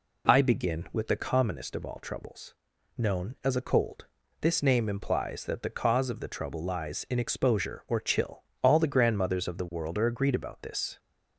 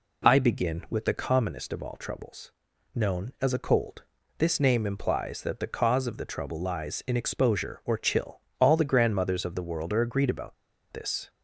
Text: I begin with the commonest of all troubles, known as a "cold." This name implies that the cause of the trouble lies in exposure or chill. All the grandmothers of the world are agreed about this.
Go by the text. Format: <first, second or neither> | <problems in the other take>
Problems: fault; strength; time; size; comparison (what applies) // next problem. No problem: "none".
first | pauses between "about" and "this"; at 10.5 s; 0.37 s long